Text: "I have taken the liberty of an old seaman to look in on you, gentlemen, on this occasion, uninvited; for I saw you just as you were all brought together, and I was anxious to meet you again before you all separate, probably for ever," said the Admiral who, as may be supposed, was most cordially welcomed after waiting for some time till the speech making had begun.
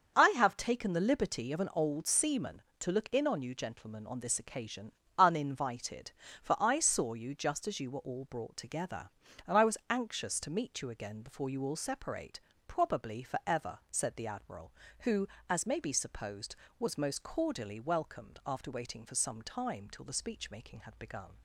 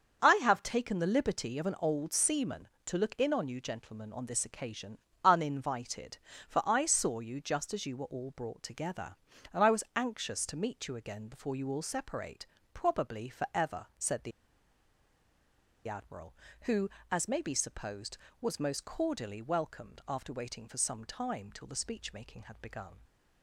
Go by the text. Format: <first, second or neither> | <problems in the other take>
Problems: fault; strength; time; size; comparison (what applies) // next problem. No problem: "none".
first | starts louder than the rest; until 1.2 s; 6.5 dB; also in the first // pauses between "the" and "Admiral"; strong; at 14.3 s; 1.5 s long